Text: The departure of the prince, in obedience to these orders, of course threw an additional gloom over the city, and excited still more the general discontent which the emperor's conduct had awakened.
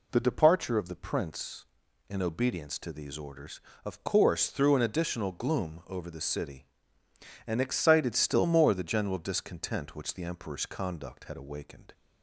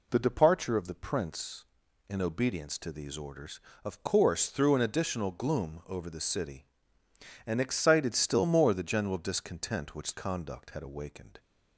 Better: first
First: none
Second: skips "the emperor's"; at 10.1 s

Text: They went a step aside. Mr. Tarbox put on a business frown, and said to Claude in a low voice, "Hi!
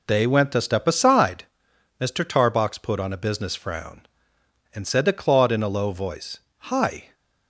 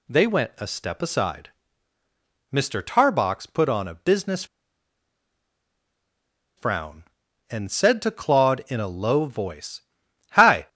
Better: first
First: none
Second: pauses between "business" and "frown"; strong; at 4.4 s; 2.1 s long

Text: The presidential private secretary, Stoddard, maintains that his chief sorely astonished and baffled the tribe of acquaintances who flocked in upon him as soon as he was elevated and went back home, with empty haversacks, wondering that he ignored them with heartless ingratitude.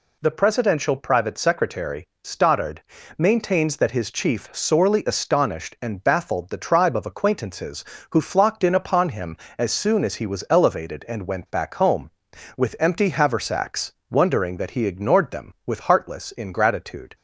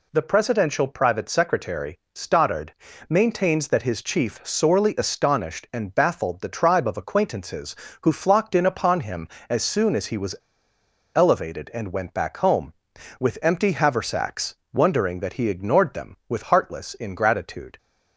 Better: first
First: none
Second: pauses between "was" and "elevated"; noticeable; at 10.3 s; 0.82 s long

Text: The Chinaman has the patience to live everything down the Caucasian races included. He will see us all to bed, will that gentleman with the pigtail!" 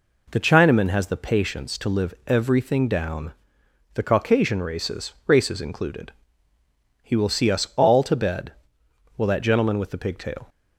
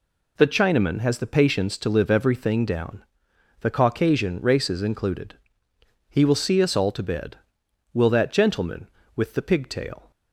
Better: second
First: pauses between "down" and "the"; noticeable; at 3.3 s; 0.62 s long // says "races" twice; at 5.2 s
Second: pauses between "down" and "the"; noticeable; at 3.0 s; 0.58 s long

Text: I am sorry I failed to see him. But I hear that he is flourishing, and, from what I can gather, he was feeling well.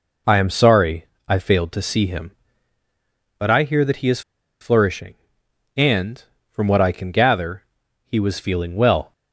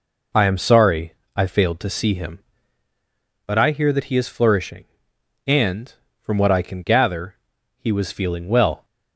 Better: second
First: pauses between "sorry" and "I"; slight; at 1.0 s; 0.20 s long // pauses between "is" and "flourishing"; at 4.2 s; 0.40 s long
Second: pauses between "sorry" and "I"; slight; at 1.1 s; 0.20 s long

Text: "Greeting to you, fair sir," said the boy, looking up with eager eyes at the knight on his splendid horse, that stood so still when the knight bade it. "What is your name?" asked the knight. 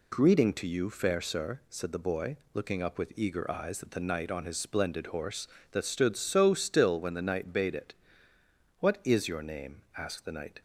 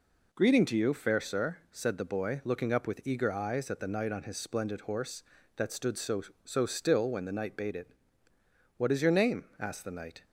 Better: first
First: none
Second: says "so" twice; at 6.4 s

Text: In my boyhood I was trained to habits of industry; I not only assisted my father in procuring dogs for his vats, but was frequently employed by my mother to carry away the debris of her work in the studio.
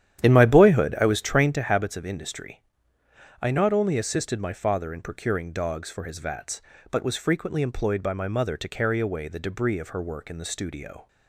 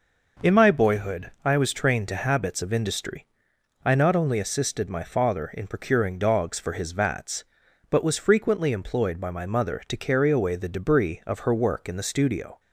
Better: second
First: starts louder than the rest; strong; until 1.6 s; 10.5 dB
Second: none

